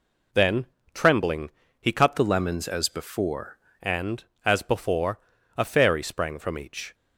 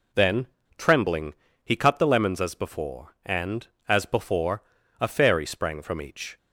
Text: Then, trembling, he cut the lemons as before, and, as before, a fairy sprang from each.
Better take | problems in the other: second | changes voice from "the" to "before"; from 2.1 to 3.5 s; 1.4 s long

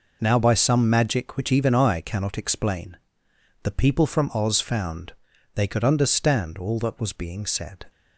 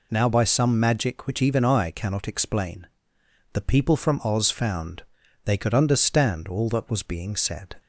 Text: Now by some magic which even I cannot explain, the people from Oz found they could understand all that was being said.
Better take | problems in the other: second | gets quieter; strong; throughout; 10 dB // pauses between "found" and "they"; at 5.1 s; 0.42 s long; also in the second

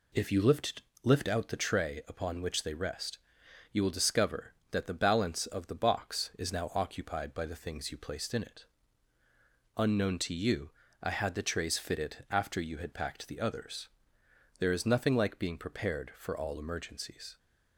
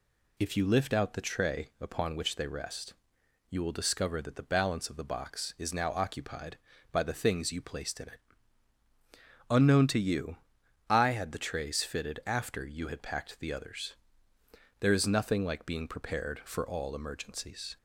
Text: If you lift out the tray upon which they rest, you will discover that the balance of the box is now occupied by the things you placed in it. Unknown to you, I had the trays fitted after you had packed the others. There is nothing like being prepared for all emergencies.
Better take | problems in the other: second | says "lift" twice; at 1.0 s

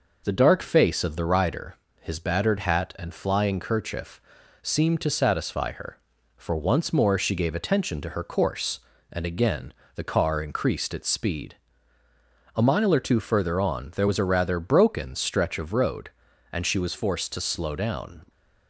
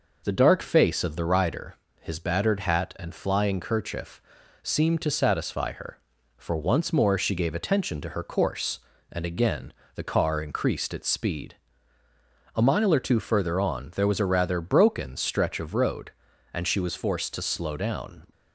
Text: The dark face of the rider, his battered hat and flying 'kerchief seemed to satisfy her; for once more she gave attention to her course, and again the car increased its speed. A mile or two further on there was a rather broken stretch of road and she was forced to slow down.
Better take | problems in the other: neither | pauses between "kerchief" and "seemed"; the same in both // pauses between "again" and "the"; slight; the same in both

